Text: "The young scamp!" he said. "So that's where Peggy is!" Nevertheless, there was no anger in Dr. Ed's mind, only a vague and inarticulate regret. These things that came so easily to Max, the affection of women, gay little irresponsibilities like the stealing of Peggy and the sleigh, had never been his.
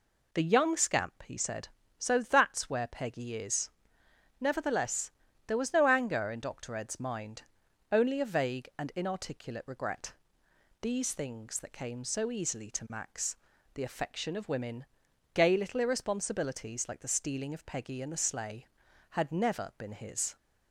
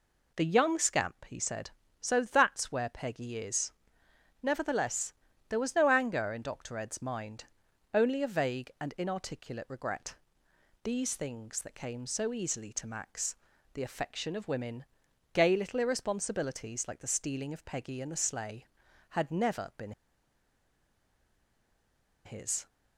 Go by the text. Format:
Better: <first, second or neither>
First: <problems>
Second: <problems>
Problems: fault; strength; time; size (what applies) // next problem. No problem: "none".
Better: first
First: none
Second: pauses between "been" and "his"; strong; at 19.9 s; 2.3 s long